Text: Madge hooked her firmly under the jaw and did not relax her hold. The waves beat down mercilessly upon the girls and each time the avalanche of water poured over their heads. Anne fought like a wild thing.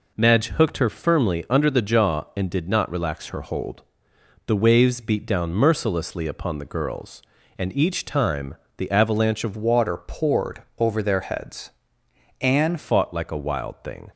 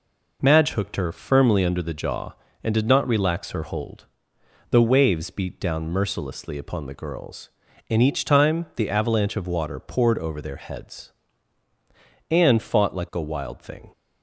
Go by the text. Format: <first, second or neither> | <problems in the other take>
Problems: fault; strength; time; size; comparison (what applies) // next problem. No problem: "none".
second | pauses between "time" and "the"; slight; at 8.5 s; 0.22 s long // changes voice from "water" to "Anne"; from 9.5 to 12.7 s; 3.2 s long // pauses between "poured" and "over"; slight; at 10.6 s; 0.16 s long